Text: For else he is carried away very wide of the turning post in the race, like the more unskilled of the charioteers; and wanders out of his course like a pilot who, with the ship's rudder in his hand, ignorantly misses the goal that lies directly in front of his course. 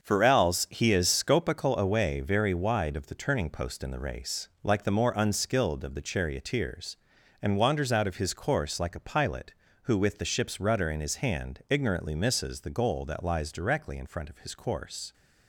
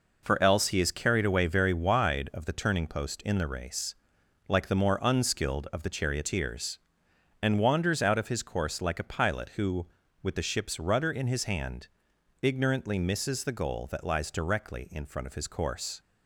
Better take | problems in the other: second | starts louder than the rest; until 1.0 s; 6.5 dB // says "scopical" for "carried"; at 1.0 s

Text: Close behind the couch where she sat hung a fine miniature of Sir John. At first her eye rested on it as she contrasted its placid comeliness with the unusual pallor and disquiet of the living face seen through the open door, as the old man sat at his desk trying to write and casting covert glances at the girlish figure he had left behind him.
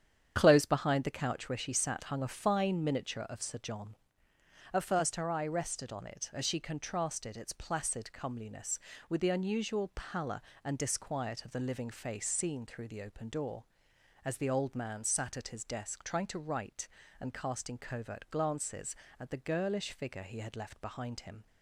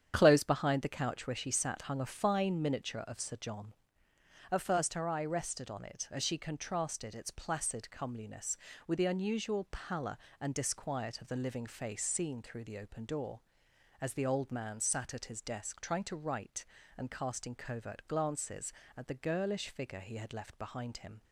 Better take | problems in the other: neither | starts louder than the rest; strong; the same in both

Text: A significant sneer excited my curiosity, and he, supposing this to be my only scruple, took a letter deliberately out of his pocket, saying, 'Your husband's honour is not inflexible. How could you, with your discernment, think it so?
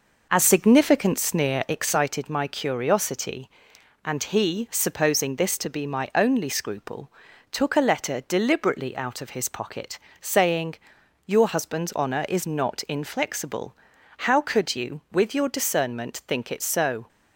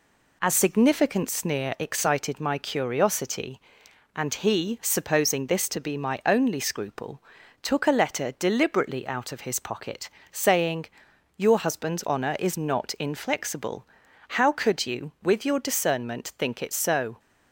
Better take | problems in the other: second | starts louder than the rest; noticeable; until 2.0 s; 5 dB

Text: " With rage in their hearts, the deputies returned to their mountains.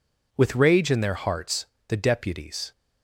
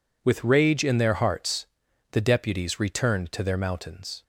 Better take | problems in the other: second | stops before "returned to their mountains"; at 2.7 s

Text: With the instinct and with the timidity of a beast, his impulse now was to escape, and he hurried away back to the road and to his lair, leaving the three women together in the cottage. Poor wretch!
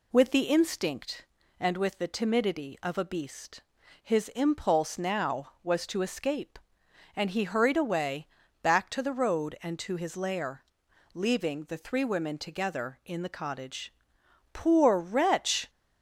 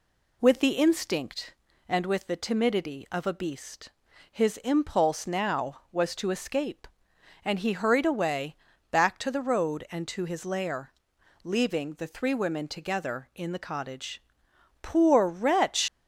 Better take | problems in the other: first | pauses between "away" and "back"; slight; at 8.5 s; 0.34 s long; slight in the first // leaves "wretch" unfinished; at 15.8 s; 105 ms

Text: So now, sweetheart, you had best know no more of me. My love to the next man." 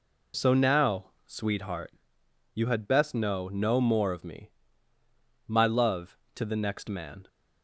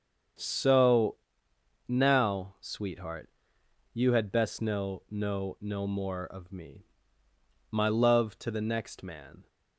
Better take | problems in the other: first | starts louder than the rest; strong; until 2.1 s; 7 dB // pauses between "So" and "now"; noticeable; at 1.1 s; 0.72 s long // says "no" twice; at 5.5 s

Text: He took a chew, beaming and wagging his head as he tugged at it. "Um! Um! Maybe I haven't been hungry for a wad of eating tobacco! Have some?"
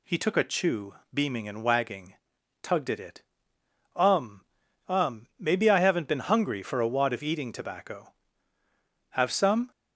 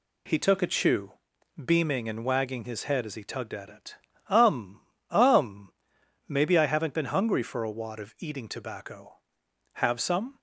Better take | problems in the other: second | skips "his head as he"; at 2.3 s

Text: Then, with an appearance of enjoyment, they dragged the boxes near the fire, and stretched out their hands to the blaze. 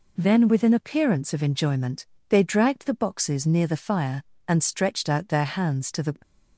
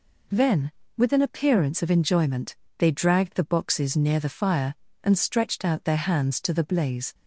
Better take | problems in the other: second | stops before "blaze"; at 6.2 s

